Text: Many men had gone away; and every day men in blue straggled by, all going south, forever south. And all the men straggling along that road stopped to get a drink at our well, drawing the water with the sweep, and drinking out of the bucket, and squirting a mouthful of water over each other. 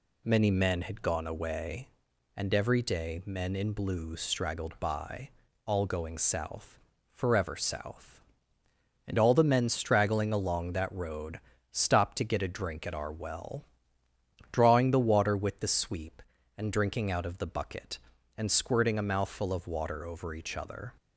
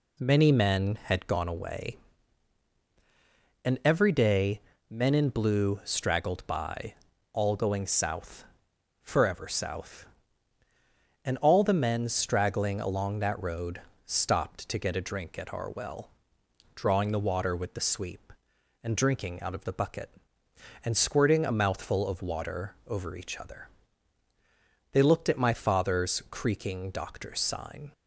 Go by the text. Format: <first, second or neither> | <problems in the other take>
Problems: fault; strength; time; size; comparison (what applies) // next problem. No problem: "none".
first | pauses between "day" and "men"; slight; at 4.6 s; 0.30 s long // pauses between "road" and "stopped"; slight; at 13.8 s; 0.26 s long; slight in the first // goes on to say "They looked at my father's creaking doctor's sign"; strong; from 24.9 s on; 3.0 s long